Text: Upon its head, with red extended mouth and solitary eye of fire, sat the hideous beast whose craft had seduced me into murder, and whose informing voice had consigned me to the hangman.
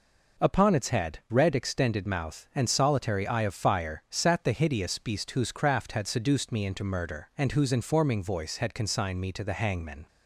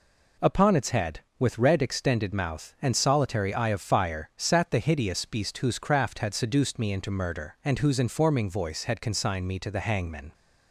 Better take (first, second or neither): second